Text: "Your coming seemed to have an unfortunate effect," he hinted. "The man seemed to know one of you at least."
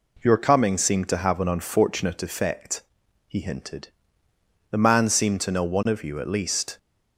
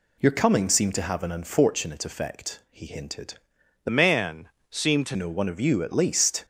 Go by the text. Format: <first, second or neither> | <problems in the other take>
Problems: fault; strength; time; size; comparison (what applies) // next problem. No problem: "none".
first | changes voice from "man" to "to"; from 3.8 to 5.1 s; 1.3 s long // pauses between "man" and "seemed"; slight; at 4.4 s; 0.20 s long